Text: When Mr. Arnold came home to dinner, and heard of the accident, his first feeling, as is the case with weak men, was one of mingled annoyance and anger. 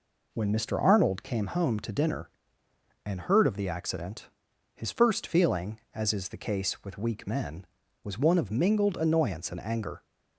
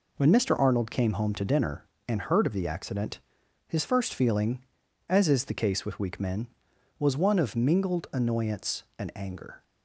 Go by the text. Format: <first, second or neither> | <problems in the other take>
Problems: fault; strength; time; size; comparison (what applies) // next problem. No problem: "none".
neither | none